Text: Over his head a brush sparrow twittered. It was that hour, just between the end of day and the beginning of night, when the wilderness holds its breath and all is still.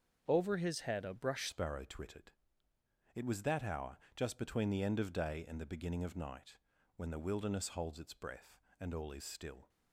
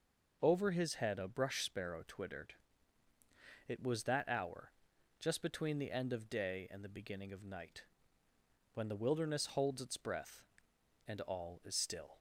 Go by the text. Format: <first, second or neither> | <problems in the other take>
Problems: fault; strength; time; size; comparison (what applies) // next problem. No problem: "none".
second | starts louder than the rest; until 1.2 s; 7 dB // changes voice at "sparrow"; from 1.4 s on; 8.2 s long